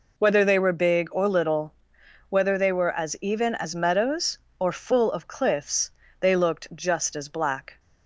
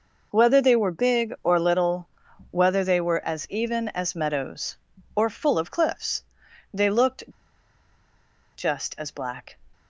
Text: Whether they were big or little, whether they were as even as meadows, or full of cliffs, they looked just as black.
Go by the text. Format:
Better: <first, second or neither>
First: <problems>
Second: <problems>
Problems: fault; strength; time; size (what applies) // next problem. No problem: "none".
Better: first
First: none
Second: pauses between "looked" and "just"; strong; at 7.2 s; 1.3 s long